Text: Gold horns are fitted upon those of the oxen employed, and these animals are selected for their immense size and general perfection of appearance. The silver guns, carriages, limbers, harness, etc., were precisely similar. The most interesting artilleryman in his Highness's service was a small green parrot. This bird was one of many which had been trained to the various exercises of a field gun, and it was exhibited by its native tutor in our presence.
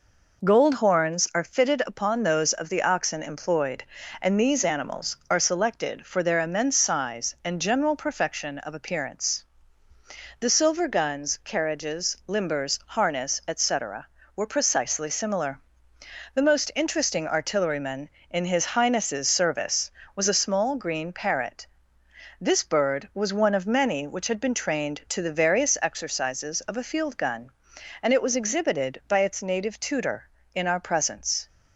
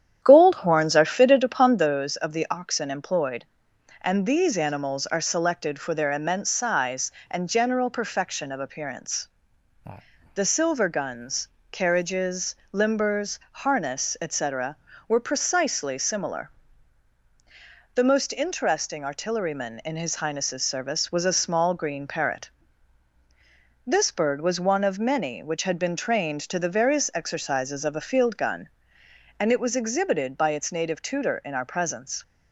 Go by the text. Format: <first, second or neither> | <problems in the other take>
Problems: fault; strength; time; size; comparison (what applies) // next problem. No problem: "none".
first | starts louder than the rest; strong; until 1.9 s; 10 dB